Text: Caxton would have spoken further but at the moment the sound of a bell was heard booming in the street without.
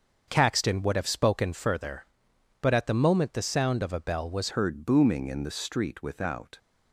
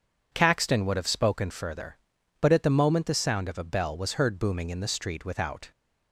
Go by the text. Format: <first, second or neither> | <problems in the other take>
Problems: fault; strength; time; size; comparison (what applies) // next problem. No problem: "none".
second | starts louder than the rest; until 1.2 s; 6.5 dB // changes voice at "heard"; from 4.5 s on; 2.0 s long